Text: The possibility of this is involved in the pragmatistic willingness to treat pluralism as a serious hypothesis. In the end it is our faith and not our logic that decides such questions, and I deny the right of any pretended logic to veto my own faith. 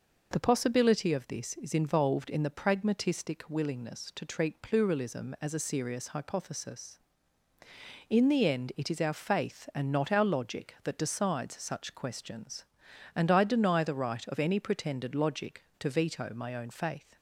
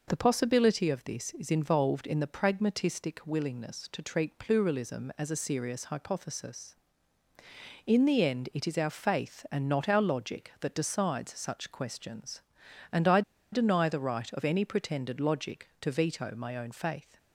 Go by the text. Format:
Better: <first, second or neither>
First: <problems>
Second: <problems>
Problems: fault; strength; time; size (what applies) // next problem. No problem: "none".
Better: first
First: none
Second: pauses between "I" and "deny"; slight; at 13.2 s; 0.31 s long